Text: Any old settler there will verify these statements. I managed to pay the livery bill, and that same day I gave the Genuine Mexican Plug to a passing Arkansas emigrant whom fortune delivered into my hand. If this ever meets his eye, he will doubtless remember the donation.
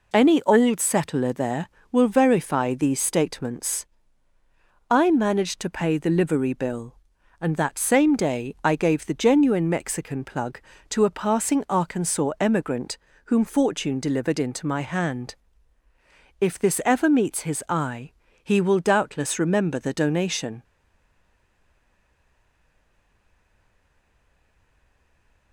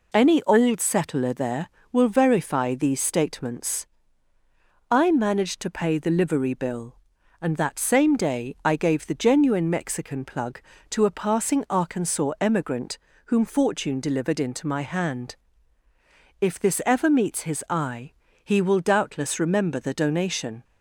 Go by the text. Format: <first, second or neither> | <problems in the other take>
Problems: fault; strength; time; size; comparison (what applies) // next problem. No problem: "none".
second | pauses between "emigrant" and "whom"; slight; at 12.9 s; 0.28 s long; slight in the second // stays silent after the last word; strong; from 20.6 s on; 4.9 s long